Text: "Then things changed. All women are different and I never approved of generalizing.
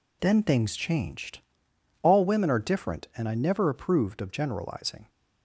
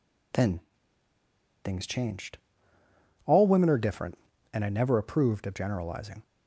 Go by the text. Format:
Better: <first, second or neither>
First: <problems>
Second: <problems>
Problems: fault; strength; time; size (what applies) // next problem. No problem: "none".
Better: first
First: none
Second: pauses between "Then" and "things"; at 0.6 s; 1.0 s long